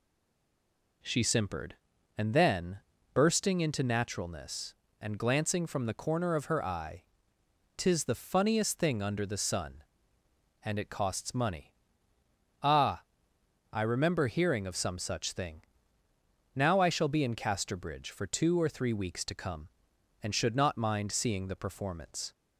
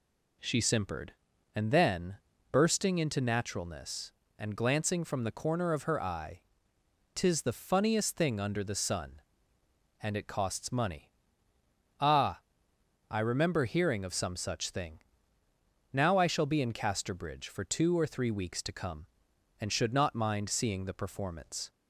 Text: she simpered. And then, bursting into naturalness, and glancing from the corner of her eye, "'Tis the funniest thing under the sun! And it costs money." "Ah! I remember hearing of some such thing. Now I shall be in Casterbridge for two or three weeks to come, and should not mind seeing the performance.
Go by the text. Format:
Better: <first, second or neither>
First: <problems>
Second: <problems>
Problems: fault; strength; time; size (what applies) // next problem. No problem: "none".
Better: second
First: stays silent before the first word; until 1.0 s; 1.0 s long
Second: none